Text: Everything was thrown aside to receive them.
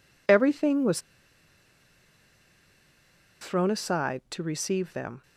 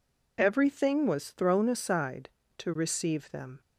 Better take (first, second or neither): second